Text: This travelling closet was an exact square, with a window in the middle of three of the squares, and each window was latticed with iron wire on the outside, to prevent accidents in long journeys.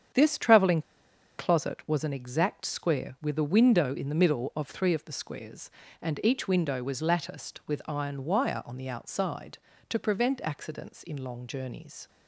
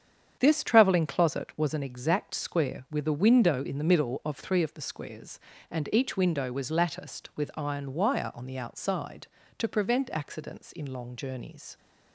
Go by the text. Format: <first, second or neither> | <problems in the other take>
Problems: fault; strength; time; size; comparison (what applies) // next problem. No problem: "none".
second | starts louder than the rest; strong; until 1.7 s; 8 dB; strong in the second // pauses between "travelling" and "closet"; noticeable; at 0.8 s; 0.57 s long